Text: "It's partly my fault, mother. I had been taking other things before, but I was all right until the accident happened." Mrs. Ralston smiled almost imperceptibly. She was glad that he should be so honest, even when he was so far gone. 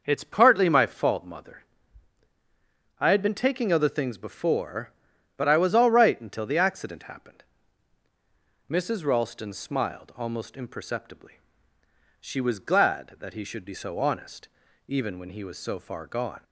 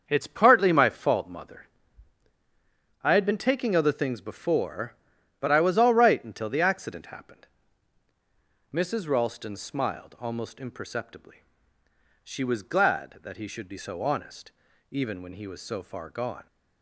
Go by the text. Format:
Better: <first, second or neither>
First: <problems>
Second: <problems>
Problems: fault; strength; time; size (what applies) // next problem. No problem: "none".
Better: first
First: none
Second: gets quieter; strong; throughout; 9 dB